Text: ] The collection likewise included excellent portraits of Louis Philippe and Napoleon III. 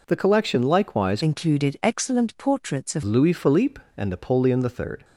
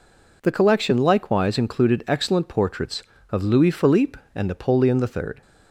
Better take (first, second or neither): second